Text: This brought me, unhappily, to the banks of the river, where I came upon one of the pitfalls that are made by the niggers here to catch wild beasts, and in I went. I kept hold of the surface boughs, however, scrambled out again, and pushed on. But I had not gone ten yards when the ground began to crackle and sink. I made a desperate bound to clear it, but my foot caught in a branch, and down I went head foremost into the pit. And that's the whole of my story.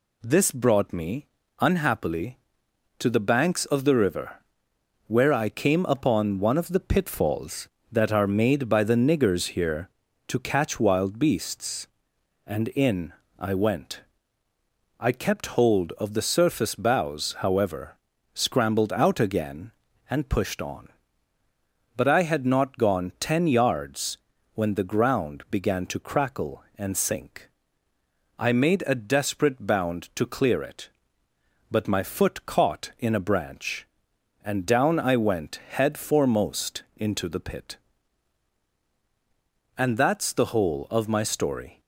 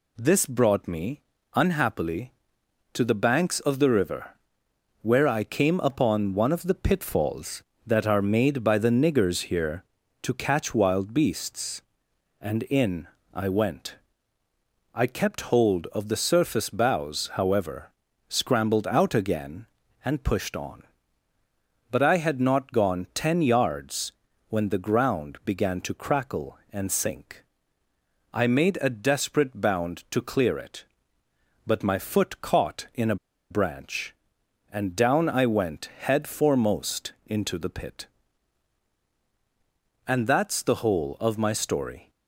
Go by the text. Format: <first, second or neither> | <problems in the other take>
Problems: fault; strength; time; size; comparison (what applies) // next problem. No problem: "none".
first | pauses between "in" and "I"; slight; at 13.0 s; 0.26 s long; slight in the first // pauses between "yards" and "when"; at 24.1 s; 0.38 s long; also in the first // pauses between "a" and "branch"; slight; at 33.1 s; 0.35 s long